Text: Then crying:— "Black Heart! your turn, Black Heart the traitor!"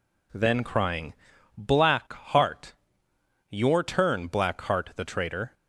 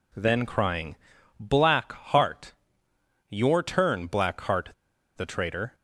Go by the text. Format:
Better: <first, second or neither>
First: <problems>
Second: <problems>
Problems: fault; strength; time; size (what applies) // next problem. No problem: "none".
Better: first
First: none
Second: pauses between "Heart" and "the"; noticeable; at 4.6 s; 0.47 s long